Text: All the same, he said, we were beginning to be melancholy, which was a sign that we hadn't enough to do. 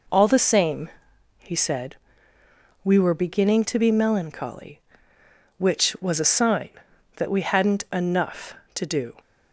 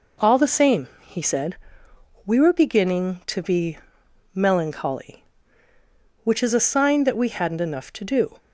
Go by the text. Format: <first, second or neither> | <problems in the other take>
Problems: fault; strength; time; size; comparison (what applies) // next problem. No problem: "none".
first | pauses between "be" and "melancholy"; noticeable; at 3.7 s; 0.56 s long // says "is" for "was"; at 6.4 s